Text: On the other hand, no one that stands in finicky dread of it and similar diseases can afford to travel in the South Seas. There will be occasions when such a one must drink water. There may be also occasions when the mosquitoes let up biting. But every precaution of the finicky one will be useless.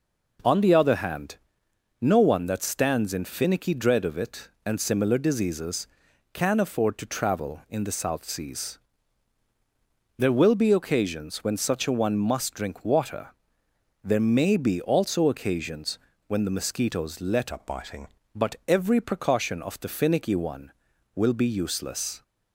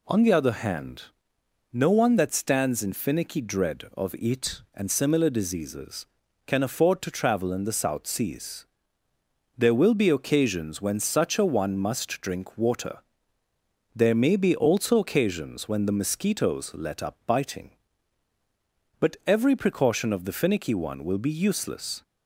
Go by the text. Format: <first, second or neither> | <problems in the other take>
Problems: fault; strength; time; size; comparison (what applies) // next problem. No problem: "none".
second | pauses between "occasions" and "when"; slight; at 15.9 s; 0.28 s long // changes voice from "up" to "biting"; from 17.5 to 18.0 s; 0.5 s long